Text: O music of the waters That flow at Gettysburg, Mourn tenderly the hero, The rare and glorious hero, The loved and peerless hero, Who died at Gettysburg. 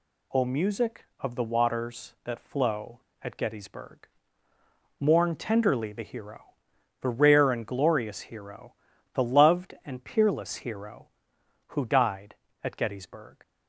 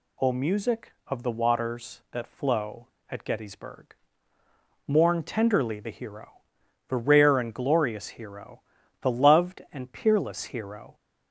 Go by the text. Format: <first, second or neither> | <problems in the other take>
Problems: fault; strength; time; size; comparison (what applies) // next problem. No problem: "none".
first | stops before "Who died at Gettysburg"; at 10.9 s